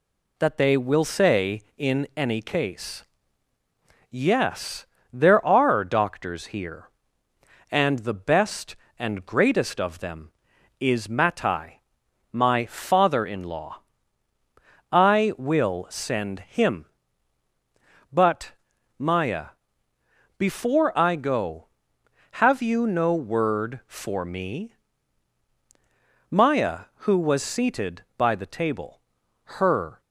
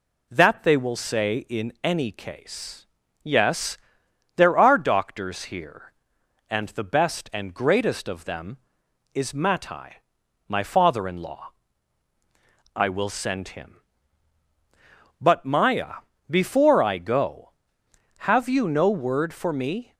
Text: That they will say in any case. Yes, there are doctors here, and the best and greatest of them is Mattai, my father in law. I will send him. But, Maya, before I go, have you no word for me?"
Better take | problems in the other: second | goes on to say "Maya who was seated by the table her"; strong; from 26.2 s on; 3.7 s long

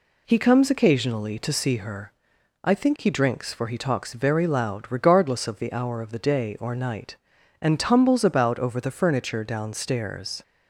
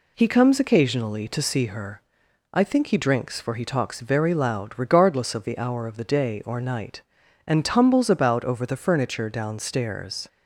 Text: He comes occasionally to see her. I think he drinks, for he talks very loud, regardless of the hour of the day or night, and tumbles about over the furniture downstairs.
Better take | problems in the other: neither | none

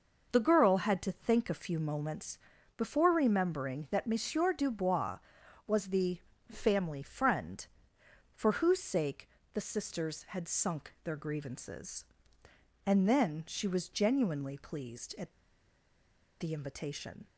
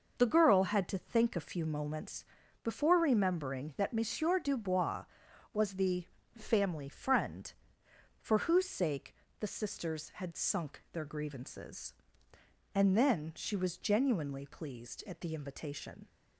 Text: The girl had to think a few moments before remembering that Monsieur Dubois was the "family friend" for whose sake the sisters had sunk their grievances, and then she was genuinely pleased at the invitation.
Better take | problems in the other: second | pauses between "moments" and "before"; at 2.3 s; 0.38 s long; also in the second // pauses between "the" and "family"; slight; at 6.1 s; 0.32 s long; slight in the second // pauses between "sake" and "the"; slight; at 9.2 s; 0.24 s long; slight in the second // pauses between "at" and "the"; at 15.3 s; 1.0 s long

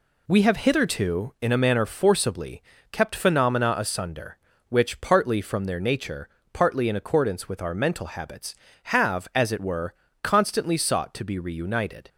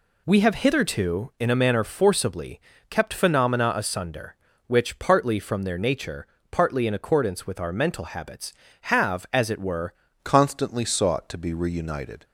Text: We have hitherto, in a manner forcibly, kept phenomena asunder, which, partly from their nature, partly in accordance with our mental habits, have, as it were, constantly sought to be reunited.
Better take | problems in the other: first | changes voice at "constantly"; from 10.2 s on; 2.0 s long

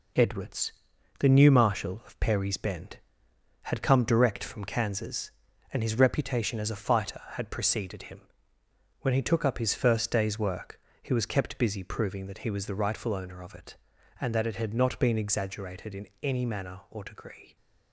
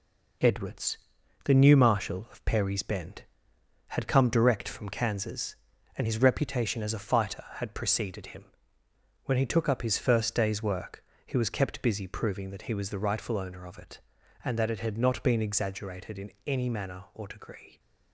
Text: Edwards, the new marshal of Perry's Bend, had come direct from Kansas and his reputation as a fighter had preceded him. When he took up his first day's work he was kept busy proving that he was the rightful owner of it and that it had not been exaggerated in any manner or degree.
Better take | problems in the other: neither | pauses between "work" and "he"; slight; the same in both // pauses between "in" and "any"; slight; the same in both

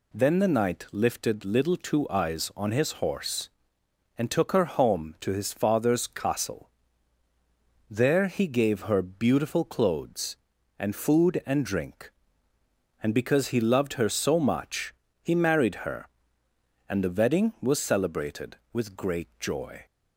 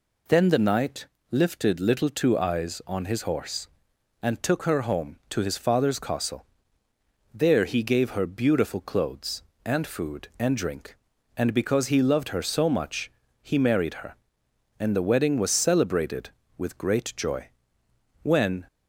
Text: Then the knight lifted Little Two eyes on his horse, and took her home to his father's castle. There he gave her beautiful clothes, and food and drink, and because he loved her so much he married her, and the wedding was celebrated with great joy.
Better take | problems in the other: first | pauses between "knight" and "lifted"; slight; at 1.0 s; 0.26 s long // pauses between "much" and "he"; slight; at 13.0 s; 0.32 s long; slight in the first // goes on to say "When"; slight; from 18.2 s on; 0.44 s long

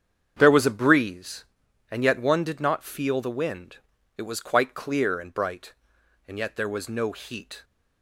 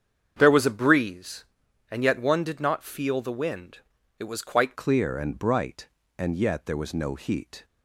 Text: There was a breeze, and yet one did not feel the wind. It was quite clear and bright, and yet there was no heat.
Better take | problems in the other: first | starts louder than the rest; strong; until 1.4 s; 7.5 dB; strong in the first // changes voice at "clear"; from 4.7 s on; 2.9 s long

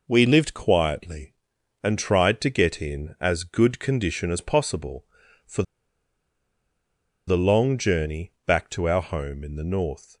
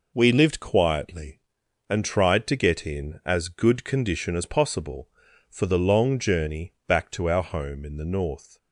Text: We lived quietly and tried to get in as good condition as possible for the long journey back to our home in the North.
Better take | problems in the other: second | pauses between "for" and "the"; strong; at 5.6 s; 1.6 s long

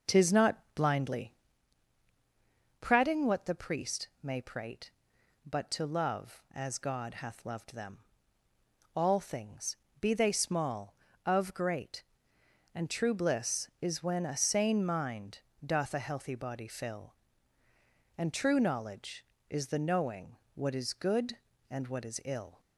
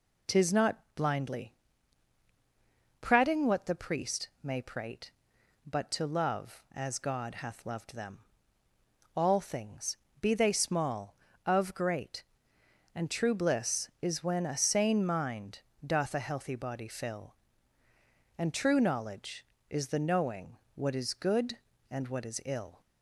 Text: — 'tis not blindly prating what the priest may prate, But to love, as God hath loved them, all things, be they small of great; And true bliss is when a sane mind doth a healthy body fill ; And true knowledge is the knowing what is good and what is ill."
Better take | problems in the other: second | starts louder than the rest; noticeable; until 1.7 s; 6 dB // pauses between "not" and "blindly"; slight; at 0.5 s; 0.16 s long; slight in the second // pauses between "blindly" and "prating"; strong; at 1.3 s; 1.4 s long; strong in the second // pauses between "mind" and "doth"; slight; at 15.4 s; 0.24 s long; slight in the second // pauses between "knowing" and "what"; slight; at 20.3 s; 0.18 s long; slight in the second

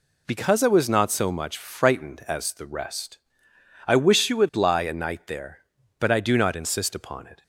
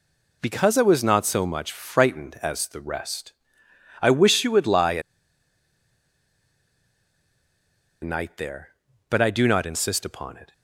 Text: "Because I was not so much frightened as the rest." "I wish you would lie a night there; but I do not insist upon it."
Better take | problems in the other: first | pauses between "a" and "night"; strong; at 5.0 s; 3.0 s long

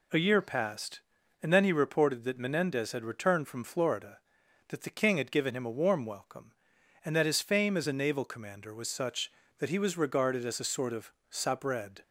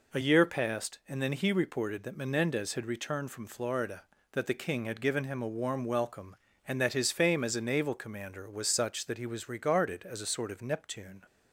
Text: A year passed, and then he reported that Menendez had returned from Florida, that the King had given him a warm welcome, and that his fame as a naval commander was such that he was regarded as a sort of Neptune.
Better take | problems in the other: second | says "Sabred" for "Neptune"; at 11.3 s

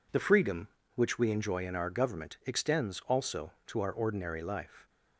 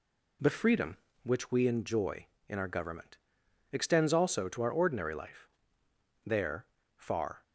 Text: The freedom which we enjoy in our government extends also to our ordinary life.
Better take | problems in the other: first | pauses between "government" and "extends"; noticeable; at 3.1 s; 0.54 s long // goes on to say "There far"; noticeable; from 6.2 s on; 1.1 s long

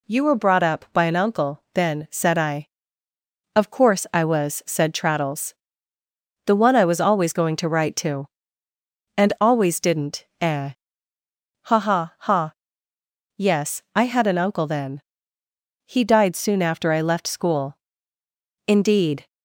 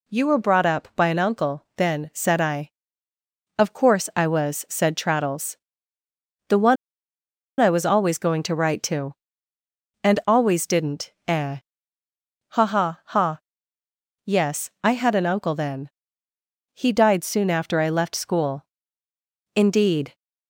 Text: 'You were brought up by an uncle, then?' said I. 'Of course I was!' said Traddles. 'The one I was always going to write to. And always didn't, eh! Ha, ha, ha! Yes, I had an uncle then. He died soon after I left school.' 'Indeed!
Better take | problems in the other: first | pauses between "one" and "I"; noticeable; at 6.7 s; 0.84 s long

